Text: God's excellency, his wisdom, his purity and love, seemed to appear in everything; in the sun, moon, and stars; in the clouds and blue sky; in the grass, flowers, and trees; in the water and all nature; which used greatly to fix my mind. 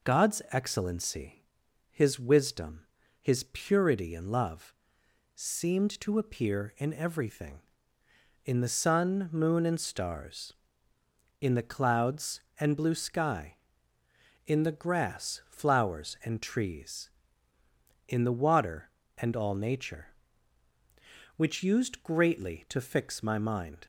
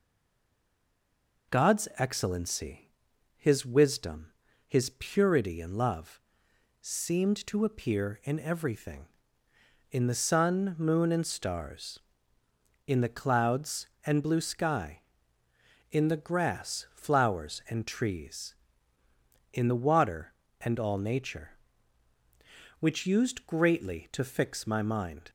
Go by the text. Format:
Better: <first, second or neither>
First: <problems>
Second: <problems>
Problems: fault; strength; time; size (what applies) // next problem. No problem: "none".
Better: first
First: none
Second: stays silent before the first word; noticeable; until 1.5 s; 1.5 s long